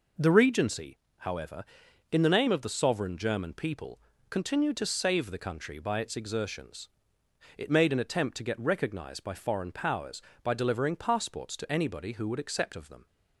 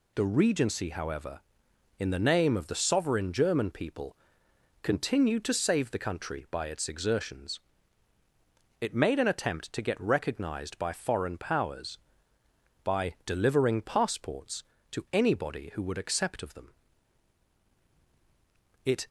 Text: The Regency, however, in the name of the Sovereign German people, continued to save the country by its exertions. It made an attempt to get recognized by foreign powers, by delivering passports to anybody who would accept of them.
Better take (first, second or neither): first